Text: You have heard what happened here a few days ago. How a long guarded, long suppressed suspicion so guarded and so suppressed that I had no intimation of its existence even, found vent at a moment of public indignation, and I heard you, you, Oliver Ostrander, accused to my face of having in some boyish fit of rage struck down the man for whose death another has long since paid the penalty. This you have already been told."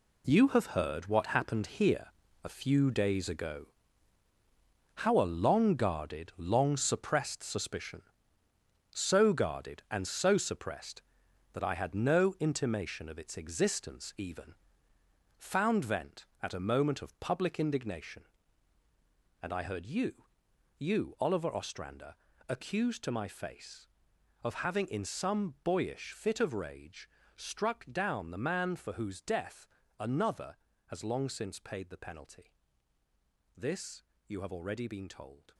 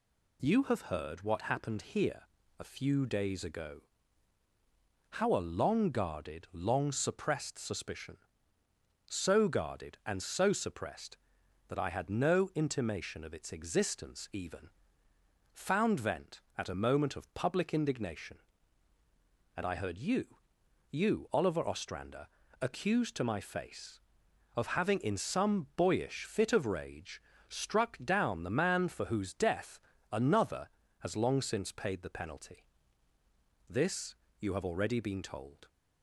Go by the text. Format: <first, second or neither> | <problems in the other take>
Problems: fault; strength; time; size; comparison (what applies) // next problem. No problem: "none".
second | gets quieter; strong; throughout; 10.5 dB // pauses between "here" and "a"; slight; at 2.0 s; 0.36 s long; slight in the second // pauses between "rage" and "struck"; slight; at 27.0 s; 0.26 s long; slight in the second // pauses between "death" and "another"; slight; at 29.6 s; 0.32 s long; slight in the second // pauses between "This" and "you"; slight; at 34.0 s; 0.24 s long; slight in the second